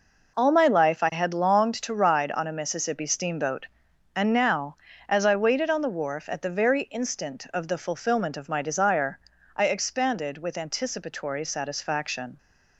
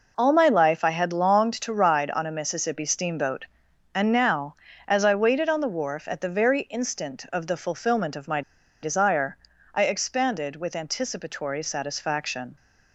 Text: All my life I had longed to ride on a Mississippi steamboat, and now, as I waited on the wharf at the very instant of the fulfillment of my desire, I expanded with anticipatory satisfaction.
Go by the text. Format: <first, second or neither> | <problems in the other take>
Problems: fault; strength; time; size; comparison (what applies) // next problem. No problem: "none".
first | pauses between "my" and "desire"; at 8.4 s; 0.42 s long